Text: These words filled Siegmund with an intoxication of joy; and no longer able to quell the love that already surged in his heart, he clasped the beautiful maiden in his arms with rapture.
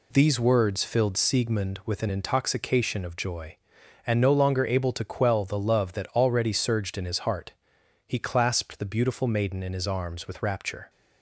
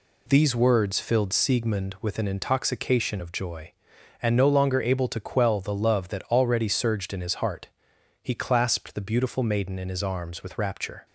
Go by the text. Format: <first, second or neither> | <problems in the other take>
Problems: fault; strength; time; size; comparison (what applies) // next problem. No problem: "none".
neither | none